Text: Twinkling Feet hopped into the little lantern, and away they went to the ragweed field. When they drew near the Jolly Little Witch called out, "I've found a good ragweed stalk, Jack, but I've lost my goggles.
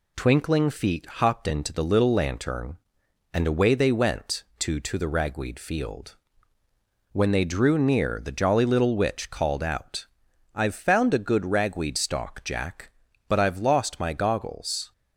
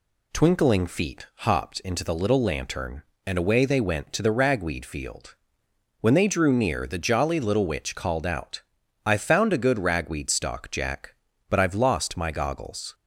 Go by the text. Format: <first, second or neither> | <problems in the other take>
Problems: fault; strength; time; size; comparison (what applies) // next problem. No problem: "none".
second | says "to" twice; at 4.7 s